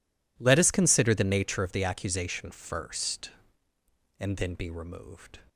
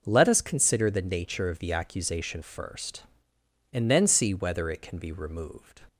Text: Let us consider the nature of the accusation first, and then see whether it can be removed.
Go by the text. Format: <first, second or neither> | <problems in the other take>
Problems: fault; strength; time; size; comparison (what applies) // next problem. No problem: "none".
second | skips "see whether it can"; at 4.5 s